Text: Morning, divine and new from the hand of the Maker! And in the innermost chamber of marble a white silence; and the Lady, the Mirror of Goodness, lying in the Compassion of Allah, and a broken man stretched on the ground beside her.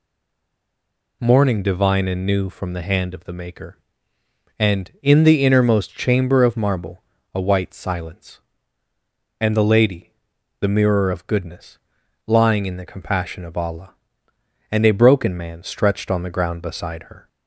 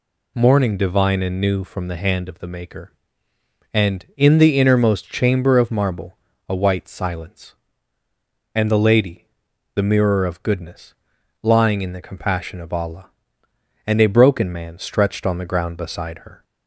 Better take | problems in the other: second | stays silent before the first word; noticeable; until 1.2 s; 1.2 s long // pauses between "marble" and "a"; slight; at 7.0 s; 0.32 s long; slight in the second

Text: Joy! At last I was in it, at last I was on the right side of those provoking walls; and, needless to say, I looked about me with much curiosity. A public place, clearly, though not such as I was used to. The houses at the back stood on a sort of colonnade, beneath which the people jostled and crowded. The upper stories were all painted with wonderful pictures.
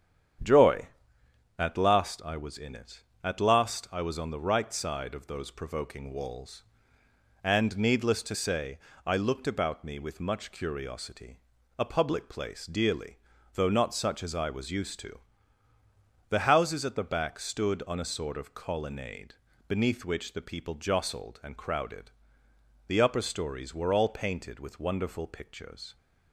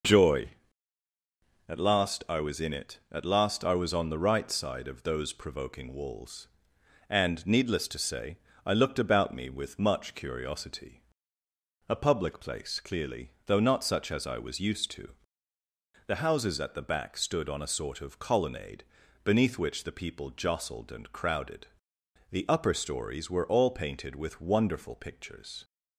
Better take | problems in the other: second | starts louder than the rest; strong; until 2.1 s; 8.5 dB // says "dearly" for "clearly"; at 12.6 s

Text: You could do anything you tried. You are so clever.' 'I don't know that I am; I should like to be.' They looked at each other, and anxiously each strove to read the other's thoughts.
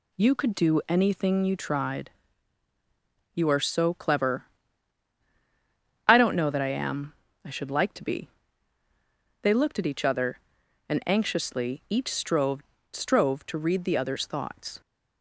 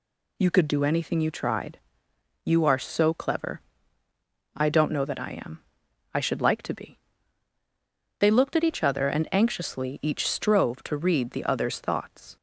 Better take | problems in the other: second | says "strove" twice; at 12.9 s

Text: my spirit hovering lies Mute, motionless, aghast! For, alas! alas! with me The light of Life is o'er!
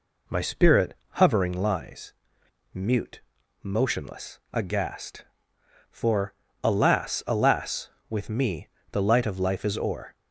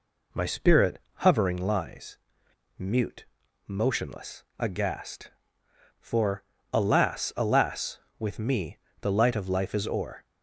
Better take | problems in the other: neither | pauses between "spirit" and "hovering"; slight; the same in both // pauses between "lies" and "Mute"; noticeable; the same in both // pauses between "me" and "The"; slight; the same in both

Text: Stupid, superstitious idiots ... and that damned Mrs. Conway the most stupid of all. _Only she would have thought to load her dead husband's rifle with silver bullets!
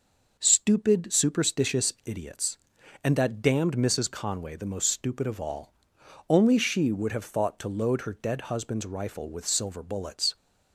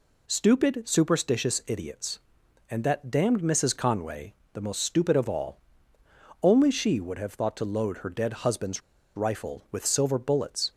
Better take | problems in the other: first | pauses between "Conway" and "the"; slight; at 4.3 s; 0.18 s long // pauses between "husband's" and "rifle"; slight; at 8.8 s; 0.35 s long

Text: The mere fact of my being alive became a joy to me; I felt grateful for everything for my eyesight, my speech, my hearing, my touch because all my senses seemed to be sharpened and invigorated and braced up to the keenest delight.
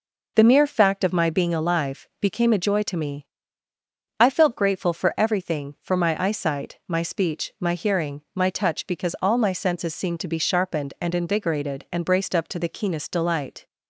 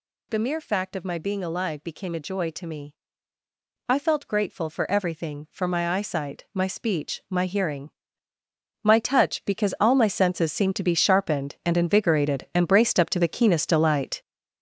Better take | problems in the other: first | gets louder; strong; throughout; 8 dB

